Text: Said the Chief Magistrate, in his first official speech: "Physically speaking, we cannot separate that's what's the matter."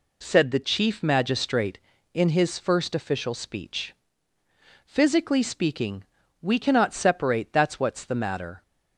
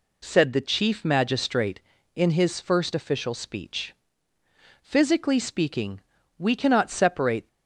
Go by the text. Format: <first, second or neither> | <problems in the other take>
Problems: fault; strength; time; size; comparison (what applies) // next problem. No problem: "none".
first | stops before "that's what's the matter"; at 7.4 s